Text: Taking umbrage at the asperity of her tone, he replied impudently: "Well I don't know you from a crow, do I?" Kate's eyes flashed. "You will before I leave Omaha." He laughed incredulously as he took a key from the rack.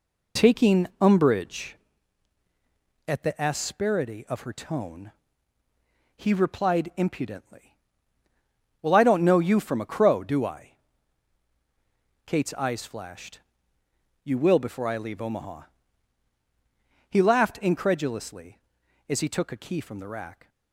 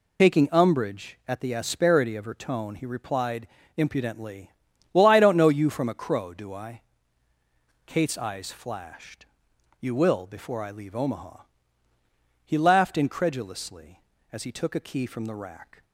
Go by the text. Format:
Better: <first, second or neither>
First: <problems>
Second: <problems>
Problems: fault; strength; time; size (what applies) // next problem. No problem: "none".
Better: first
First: none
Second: loses the start of "Taking"; at 0.1 s; 60 ms // pauses between "replied" and "impudently"; slight; at 3.4 s; 0.30 s long